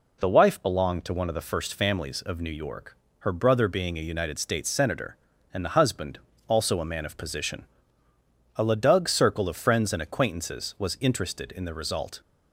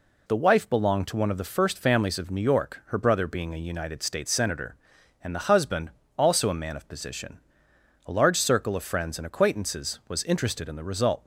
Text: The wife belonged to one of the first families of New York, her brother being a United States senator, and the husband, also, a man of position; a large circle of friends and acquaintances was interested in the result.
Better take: second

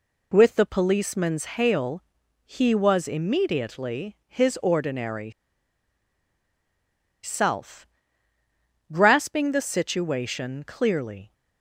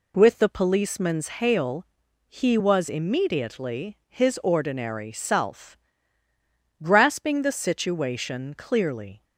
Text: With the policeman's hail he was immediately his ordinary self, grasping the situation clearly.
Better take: second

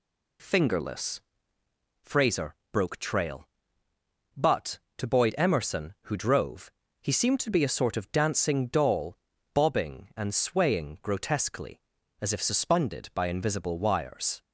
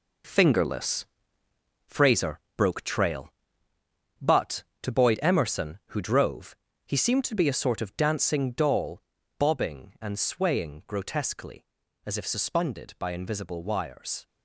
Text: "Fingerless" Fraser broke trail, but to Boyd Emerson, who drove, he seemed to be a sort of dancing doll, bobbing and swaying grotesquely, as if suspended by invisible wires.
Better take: first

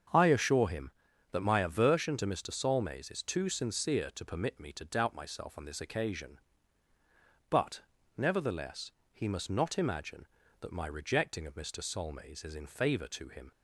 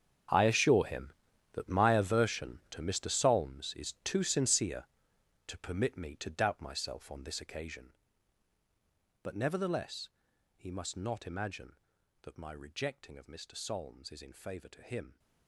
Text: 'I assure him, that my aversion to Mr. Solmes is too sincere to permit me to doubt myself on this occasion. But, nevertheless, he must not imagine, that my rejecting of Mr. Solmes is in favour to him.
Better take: first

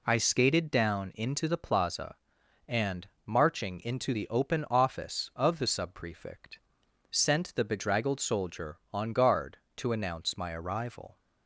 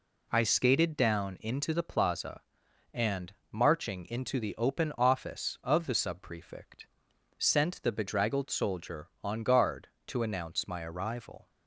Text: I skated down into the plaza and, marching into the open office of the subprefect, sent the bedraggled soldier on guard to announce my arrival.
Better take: neither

